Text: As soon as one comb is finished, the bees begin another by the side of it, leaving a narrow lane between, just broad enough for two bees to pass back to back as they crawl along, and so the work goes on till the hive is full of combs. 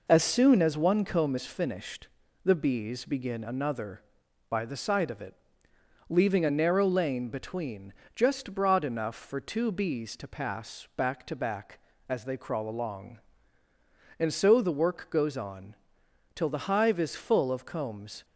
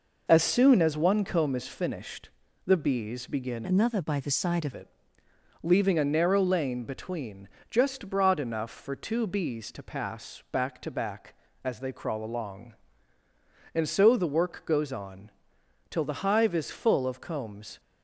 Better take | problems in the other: first | changes voice from "another" to "of"; from 3.6 to 4.7 s; 1.1 s long // pauses between "on" and "till"; noticeable; at 15.2 s; 0.60 s long; noticeable in the first

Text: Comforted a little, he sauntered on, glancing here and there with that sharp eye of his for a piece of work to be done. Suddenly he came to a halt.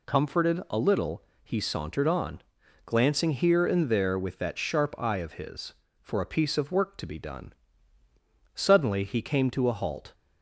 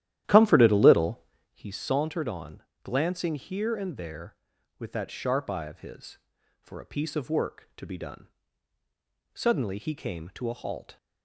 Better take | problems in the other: first | starts louder than the rest; strong; until 1.6 s; 12.5 dB

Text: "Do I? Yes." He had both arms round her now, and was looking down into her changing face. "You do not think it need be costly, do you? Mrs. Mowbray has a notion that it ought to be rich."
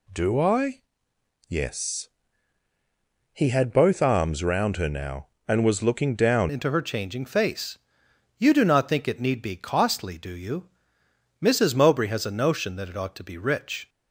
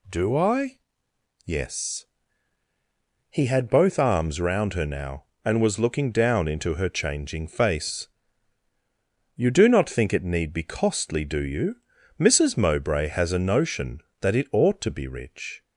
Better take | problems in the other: second | changes voice at "into"; from 6.5 s on; 7.3 s long

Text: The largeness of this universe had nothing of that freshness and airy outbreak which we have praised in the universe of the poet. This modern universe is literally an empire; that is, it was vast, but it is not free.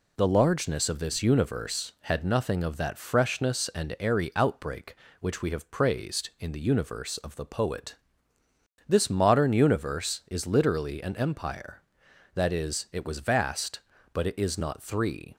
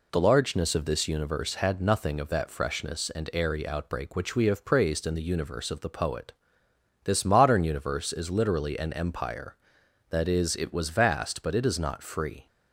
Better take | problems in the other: second | says "three" for "free"; at 14.8 s

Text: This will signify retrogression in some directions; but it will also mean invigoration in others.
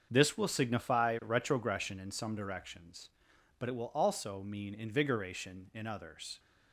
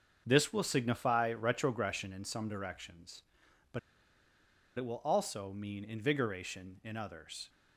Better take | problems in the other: first | starts louder than the rest; until 1.2 s; 7 dB; also in the first // pauses between "but" and "it"; noticeable; at 3.7 s; 0.97 s long

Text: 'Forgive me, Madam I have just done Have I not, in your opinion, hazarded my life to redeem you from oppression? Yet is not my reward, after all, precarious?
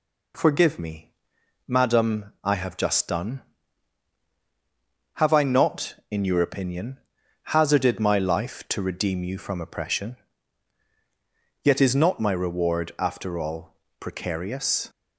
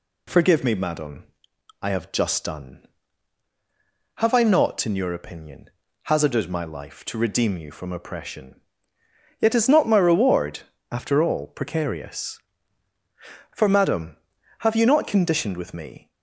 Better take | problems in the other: first | pauses between "Madam" and "I"; noticeable; at 1.2 s; 0.56 s long // goes on to say "For Madam have you not conditioned with me"; strong; from 13.5 s on; 2.5 s long

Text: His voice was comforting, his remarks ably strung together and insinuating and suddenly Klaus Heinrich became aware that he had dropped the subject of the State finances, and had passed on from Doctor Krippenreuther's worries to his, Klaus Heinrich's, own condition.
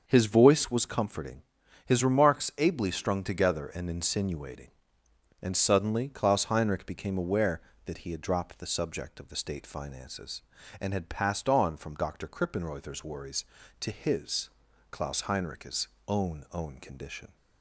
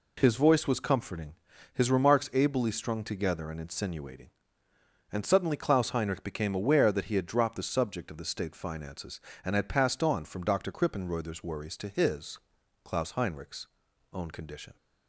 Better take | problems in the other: second | starts louder than the rest; until 1.0 s; 6.5 dB // says "own" twice; at 16.5 s

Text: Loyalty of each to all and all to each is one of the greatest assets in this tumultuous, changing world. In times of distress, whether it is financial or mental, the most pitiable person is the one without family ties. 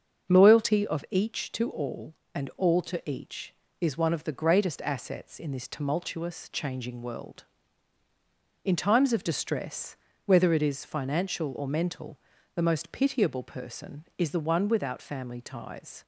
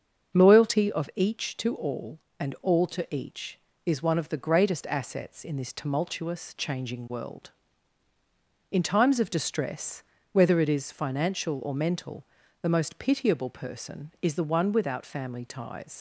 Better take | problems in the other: first | starts louder than the rest; until 1.4 s; 6.5 dB; also in the first // leaves "ties" unfinished; at 15.9 s; 60 ms

